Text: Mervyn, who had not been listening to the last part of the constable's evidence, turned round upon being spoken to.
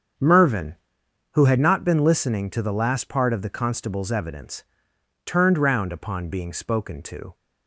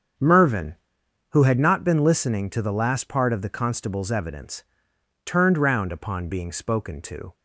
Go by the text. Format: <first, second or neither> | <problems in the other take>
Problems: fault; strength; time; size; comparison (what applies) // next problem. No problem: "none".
neither | starts louder than the rest; strong; the same in both